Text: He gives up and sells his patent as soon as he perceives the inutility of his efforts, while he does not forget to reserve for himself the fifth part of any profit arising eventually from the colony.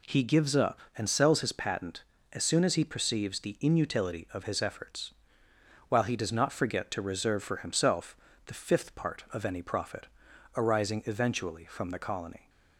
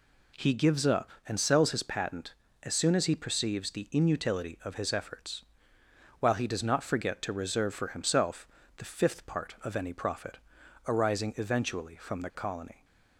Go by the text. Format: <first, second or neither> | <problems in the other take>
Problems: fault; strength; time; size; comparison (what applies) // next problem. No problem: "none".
neither | pauses between "himself" and "the"; slight; the same in both // pauses between "profit" and "arising"; noticeable; the same in both